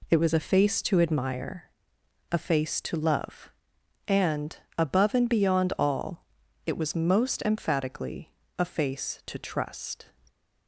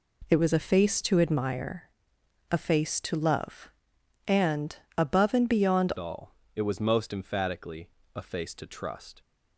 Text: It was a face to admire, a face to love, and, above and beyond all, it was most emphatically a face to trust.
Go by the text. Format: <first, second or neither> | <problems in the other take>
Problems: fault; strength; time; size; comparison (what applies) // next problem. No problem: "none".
first | changes voice at "all"; from 5.9 s on; 3.3 s long // pauses between "emphatically" and "a"; slight; at 7.8 s; 0.26 s long; slight in the first